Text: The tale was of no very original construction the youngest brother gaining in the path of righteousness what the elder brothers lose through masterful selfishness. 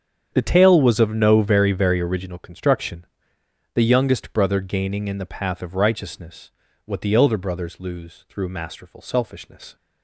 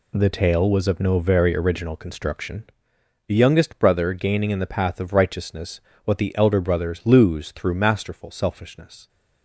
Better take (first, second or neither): second